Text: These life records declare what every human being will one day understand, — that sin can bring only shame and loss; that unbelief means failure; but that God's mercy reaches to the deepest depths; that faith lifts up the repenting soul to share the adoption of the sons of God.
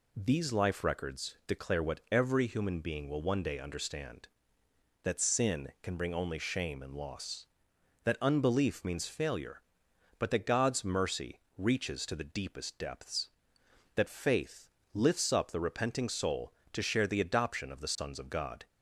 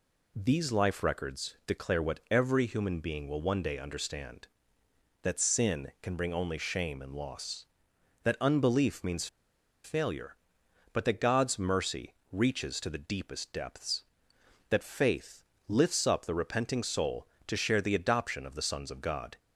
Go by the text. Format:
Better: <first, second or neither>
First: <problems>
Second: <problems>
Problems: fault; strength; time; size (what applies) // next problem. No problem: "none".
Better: first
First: pauses between "mercy" and "reaches"; slight; at 11.4 s; 0.16 s long // pauses between "faith" and "lifts"; slight; at 14.6 s; 0.24 s long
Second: pauses between "means" and "failure"; noticeable; at 9.2 s; 0.57 s long // pauses between "mercy" and "reaches"; slight; at 12.1 s; 0.16 s long // pauses between "faith" and "lifts"; slight; at 15.4 s; 0.24 s long